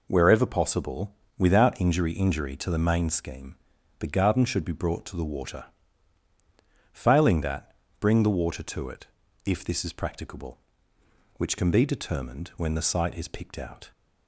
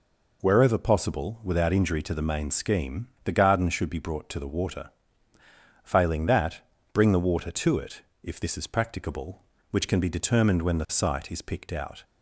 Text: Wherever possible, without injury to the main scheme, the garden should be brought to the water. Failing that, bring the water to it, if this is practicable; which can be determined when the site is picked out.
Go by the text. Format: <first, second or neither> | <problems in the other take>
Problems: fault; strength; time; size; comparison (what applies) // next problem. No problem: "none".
second | says "injury" twice; at 2.1 s